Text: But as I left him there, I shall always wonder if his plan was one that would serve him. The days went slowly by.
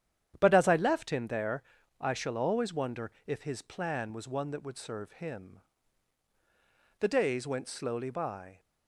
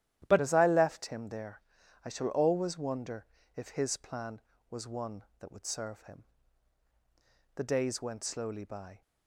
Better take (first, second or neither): first